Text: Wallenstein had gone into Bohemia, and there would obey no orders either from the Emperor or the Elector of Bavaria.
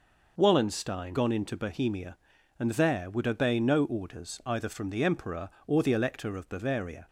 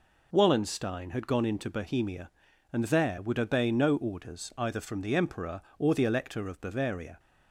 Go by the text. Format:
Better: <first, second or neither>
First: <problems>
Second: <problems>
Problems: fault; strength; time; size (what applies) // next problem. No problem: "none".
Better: second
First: skips "had"; at 1.1 s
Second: none